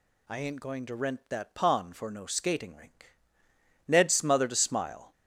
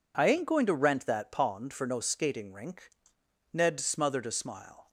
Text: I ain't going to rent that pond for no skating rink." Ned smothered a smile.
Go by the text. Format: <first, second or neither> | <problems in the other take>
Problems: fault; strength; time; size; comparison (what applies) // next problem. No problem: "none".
neither | none